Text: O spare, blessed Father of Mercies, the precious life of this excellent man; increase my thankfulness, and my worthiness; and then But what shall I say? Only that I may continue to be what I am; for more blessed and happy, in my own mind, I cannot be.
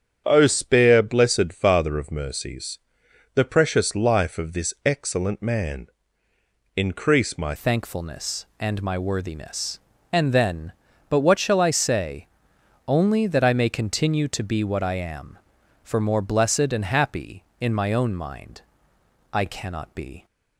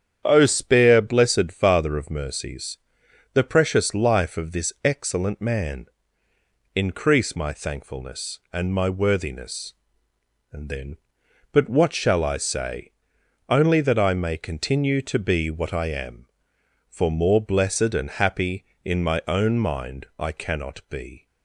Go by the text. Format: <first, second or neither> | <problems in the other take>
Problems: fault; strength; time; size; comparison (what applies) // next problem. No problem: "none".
second | starts louder than the rest; strong; until 1.2 s; 8.5 dB; strong in the second // changes voice at "thankfulness"; from 7.5 s on; 12.7 s long